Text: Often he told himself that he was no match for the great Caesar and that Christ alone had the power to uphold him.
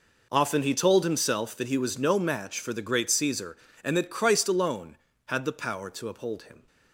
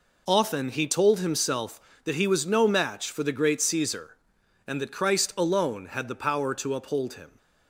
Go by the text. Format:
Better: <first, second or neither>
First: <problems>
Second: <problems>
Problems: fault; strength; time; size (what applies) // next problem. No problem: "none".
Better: neither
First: none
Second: none